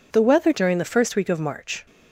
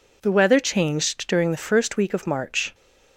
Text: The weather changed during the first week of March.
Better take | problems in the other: second | skips "changed"; at 0.5 s

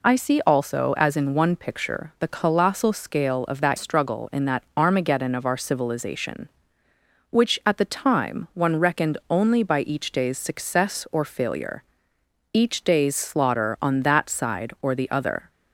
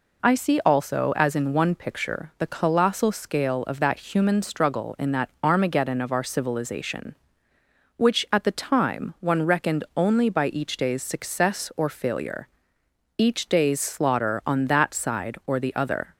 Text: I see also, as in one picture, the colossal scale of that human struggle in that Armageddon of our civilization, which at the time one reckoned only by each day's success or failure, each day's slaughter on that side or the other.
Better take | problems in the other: second | skips "human"; at 3.7 s

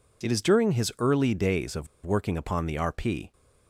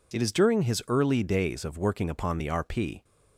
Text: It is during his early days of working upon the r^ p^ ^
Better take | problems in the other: second | pauses between "of" and "working"; slight; at 1.8 s; 0.19 s long

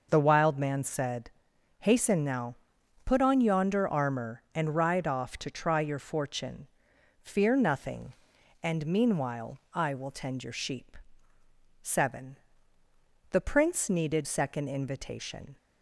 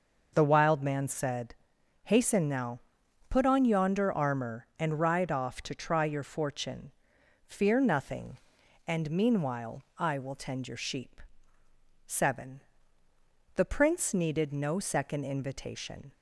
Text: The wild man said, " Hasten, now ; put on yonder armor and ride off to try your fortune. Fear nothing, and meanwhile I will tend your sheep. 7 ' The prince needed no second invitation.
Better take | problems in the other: second | skips "no"; at 14.2 s

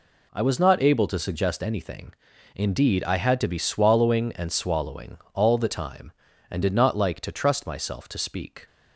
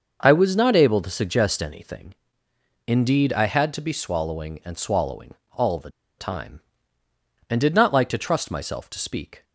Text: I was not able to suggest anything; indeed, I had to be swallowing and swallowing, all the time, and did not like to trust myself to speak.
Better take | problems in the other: first | starts louder than the rest; until 1.2 s; 6 dB // pauses between "the" and "time"; slight; at 5.8 s; 0.28 s long

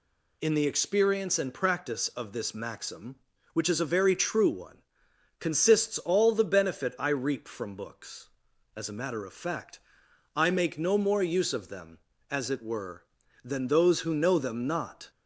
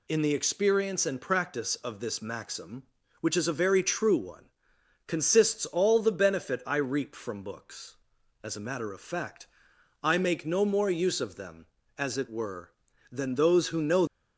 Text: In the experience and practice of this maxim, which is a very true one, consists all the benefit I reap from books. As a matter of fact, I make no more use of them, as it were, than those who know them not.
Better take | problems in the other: first | stops before "them not"; at 14.0 s

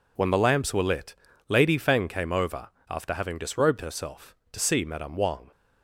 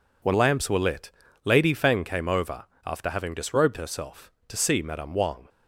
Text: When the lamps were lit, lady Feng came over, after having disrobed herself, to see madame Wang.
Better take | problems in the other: first | skips "the"; at 0.3 s

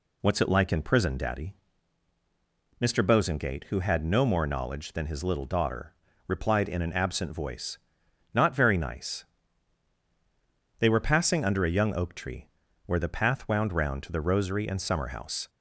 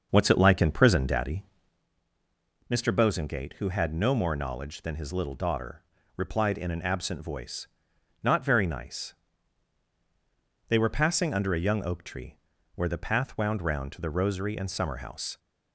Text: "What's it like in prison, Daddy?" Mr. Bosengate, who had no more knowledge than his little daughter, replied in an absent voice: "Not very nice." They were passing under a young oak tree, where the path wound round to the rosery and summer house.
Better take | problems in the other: first | starts louder than the rest; until 1.9 s; 6 dB

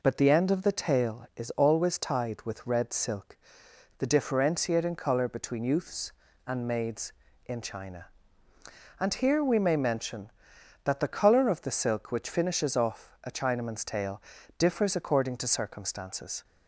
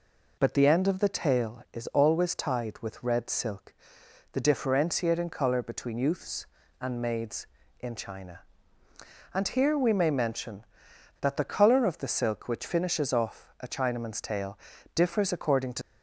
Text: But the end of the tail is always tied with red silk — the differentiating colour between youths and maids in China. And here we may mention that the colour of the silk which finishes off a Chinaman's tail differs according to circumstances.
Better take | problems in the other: first | pauses between "tail" and "differs"; slight; at 14.5 s; 0.36 s long; slight in the first // stops before "circumstances"; at 15.8 s

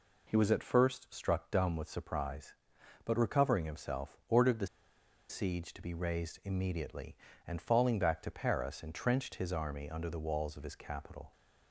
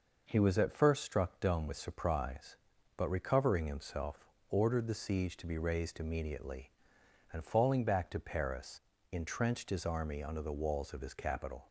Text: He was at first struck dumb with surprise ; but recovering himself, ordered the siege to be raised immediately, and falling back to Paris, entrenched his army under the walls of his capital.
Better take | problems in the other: second | pauses between "the" and "siege"; noticeable; at 4.6 s; 0.63 s long

